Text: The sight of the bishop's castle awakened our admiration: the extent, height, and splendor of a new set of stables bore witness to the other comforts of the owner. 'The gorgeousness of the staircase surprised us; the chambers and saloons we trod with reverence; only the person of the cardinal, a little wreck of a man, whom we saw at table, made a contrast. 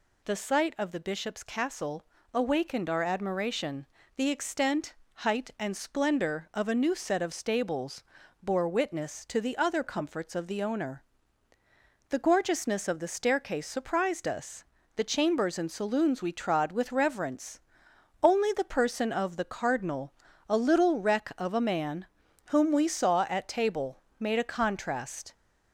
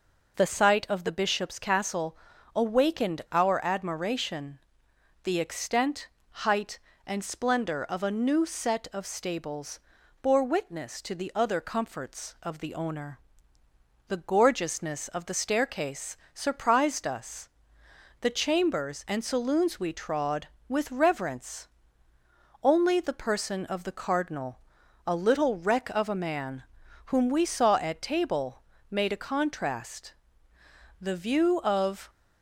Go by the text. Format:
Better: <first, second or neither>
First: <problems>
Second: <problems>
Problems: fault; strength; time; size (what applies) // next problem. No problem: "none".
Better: first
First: pauses between "castle" and "awakened"; slight; at 2.0 s; 0.28 s long // pauses between "stables" and "bore"; slight; at 8.0 s; 0.36 s long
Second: pauses between "castle" and "awakened"; slight; at 2.1 s; 0.36 s long // pauses between "stables" and "bore"; at 9.7 s; 0.42 s long // pauses between "staircase" and "surprised"; slight; at 16.1 s; 0.20 s long // goes on to say "The view of"; noticeable; from 30.9 s on; 1.1 s long